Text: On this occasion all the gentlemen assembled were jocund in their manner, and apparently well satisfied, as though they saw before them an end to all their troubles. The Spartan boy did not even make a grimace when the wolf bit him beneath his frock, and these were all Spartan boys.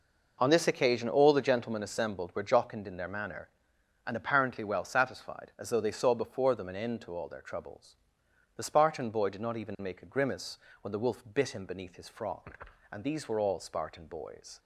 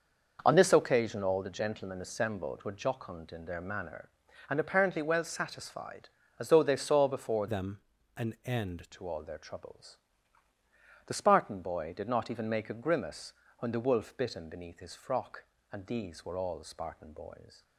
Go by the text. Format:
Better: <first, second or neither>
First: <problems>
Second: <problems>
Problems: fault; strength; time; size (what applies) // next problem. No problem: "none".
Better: first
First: pauses between "grimace" and "when"; slight; at 10.5 s; 0.22 s long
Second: changes voice from "them" to "end"; from 7.4 to 8.8 s; 1.4 s long // pauses between "them" and "an"; at 7.7 s; 0.38 s long // pauses between "grimace" and "when"; slight; at 13.3 s; 0.24 s long